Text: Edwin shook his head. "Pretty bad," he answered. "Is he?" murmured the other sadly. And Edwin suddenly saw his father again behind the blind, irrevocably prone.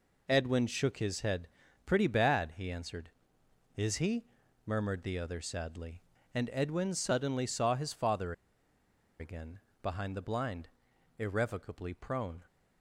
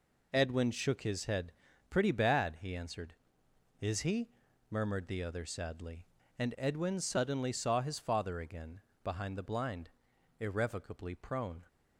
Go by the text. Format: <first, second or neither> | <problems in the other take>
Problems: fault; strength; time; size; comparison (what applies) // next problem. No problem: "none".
second | pauses between "father" and "again"; noticeable; at 8.3 s; 0.87 s long // pauses between "again" and "behind"; slight; at 9.5 s; 0.22 s long; slight in the second